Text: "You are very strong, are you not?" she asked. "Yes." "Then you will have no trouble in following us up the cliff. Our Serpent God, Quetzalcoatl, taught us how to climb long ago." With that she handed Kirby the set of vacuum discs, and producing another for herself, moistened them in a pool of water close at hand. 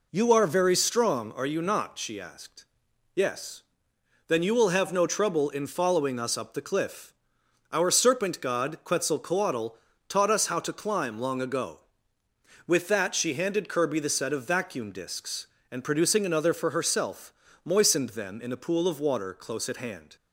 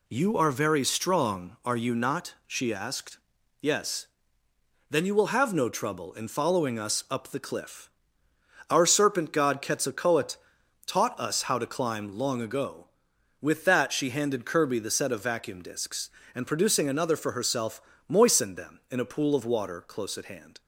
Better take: neither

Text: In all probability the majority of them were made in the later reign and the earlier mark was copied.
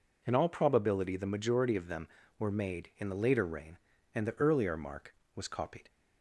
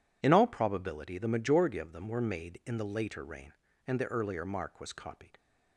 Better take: neither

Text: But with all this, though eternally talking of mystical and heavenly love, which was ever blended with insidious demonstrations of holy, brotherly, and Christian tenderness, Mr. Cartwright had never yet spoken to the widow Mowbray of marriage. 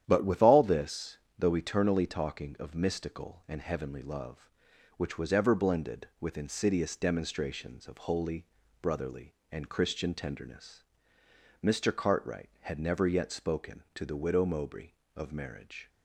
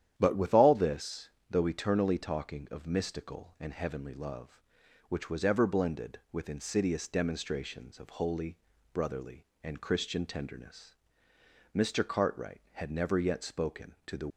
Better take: first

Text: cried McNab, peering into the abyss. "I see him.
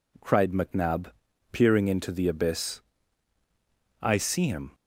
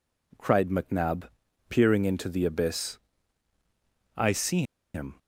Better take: first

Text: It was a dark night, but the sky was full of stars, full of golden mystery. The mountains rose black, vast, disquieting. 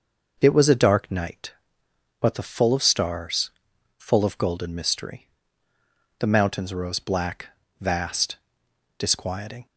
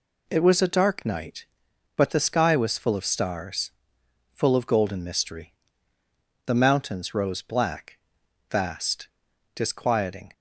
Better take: second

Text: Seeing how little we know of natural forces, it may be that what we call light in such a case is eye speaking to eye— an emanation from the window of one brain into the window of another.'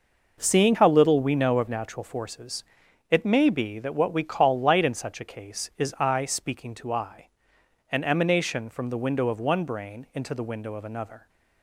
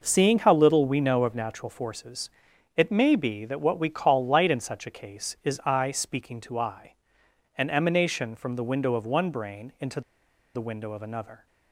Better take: first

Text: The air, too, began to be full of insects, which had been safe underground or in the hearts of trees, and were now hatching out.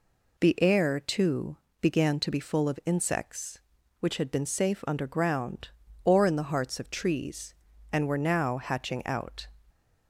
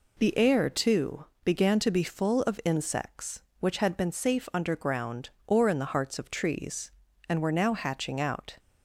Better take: neither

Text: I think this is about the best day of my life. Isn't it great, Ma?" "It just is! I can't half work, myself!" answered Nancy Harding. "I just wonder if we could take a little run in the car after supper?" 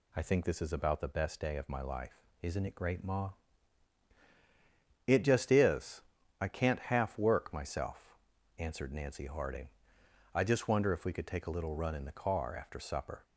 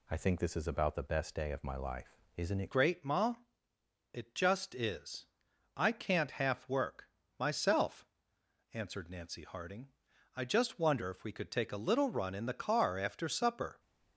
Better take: first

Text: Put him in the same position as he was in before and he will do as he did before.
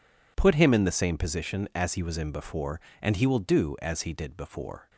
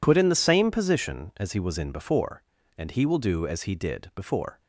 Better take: first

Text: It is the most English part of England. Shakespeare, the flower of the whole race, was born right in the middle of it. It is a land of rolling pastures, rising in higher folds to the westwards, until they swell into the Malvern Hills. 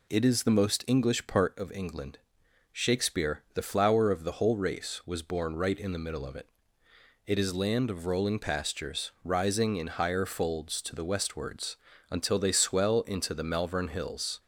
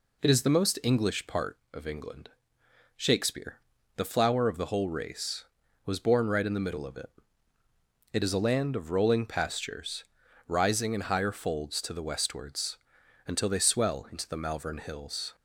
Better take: second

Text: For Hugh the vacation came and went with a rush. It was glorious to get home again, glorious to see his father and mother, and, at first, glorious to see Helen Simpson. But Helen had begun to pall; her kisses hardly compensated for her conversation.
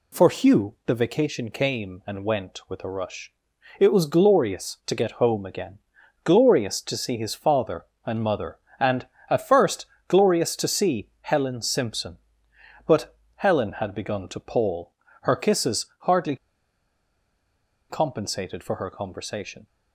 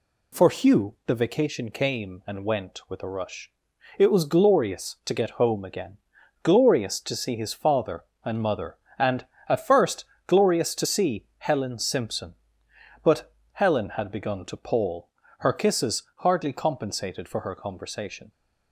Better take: second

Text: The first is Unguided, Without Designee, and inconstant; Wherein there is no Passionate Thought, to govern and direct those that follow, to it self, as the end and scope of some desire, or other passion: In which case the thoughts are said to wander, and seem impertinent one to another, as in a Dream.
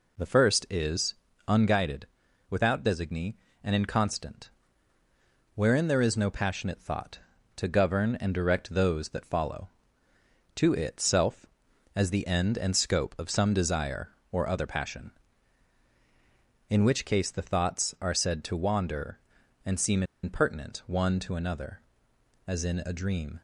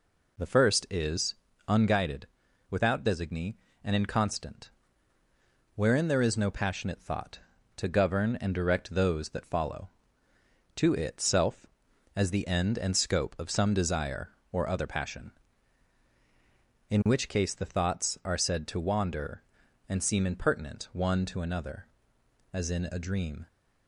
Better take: second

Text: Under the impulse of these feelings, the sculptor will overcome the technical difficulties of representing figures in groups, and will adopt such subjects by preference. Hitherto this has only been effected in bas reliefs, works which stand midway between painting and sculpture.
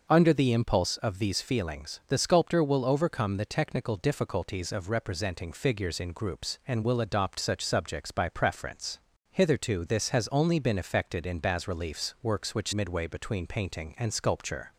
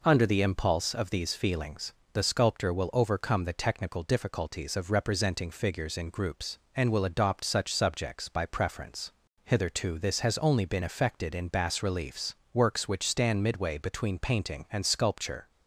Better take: second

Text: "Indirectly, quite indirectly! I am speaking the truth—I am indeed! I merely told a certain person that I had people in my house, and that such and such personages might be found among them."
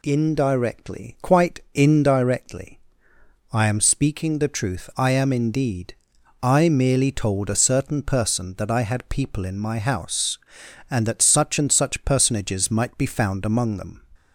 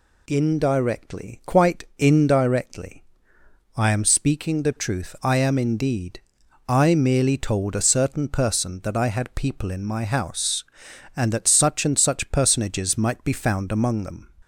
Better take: neither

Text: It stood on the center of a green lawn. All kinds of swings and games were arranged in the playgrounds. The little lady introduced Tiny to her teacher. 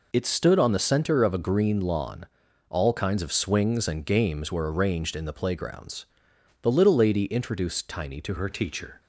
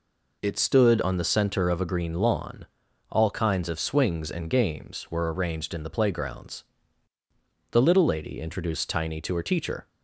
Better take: second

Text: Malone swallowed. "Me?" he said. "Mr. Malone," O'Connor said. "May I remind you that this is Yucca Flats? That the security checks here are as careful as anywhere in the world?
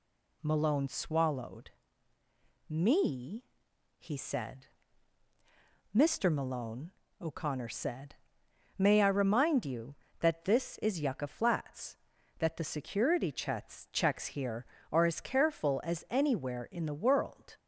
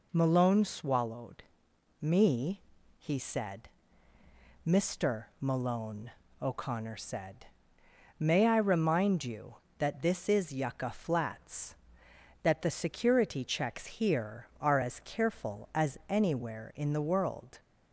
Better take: second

